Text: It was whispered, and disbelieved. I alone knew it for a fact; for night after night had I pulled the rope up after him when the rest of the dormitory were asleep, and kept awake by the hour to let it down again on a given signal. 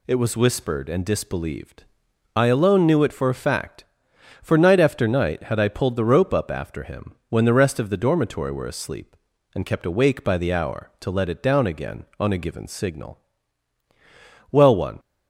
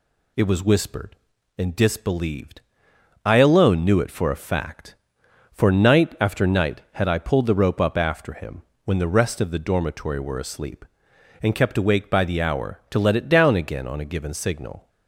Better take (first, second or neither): second